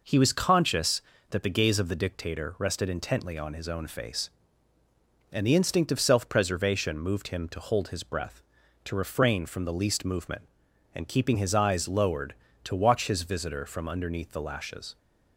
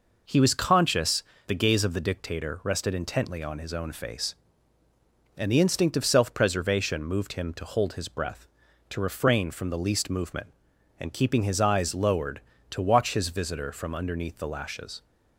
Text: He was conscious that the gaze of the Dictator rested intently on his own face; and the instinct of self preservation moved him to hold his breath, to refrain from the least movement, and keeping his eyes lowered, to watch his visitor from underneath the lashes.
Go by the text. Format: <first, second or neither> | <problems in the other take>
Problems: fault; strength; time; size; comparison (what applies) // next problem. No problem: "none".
first | skips "that"; at 1.3 s